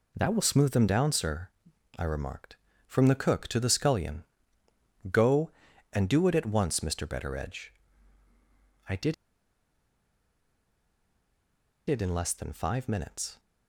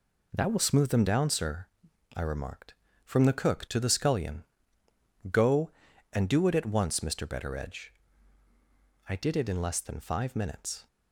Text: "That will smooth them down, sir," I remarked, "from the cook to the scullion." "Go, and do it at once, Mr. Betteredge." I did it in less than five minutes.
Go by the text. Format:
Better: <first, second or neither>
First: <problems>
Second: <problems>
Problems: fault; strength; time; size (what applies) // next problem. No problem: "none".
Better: second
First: pauses between "did" and "it"; strong; at 9.1 s; 2.7 s long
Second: none